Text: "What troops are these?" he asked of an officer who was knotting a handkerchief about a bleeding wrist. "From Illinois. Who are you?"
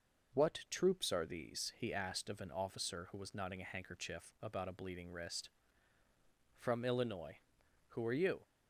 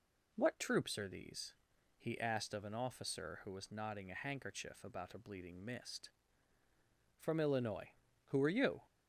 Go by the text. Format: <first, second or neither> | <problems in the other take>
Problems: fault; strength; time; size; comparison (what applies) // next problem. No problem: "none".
first | says "mist" for "wrist"; at 5.6 s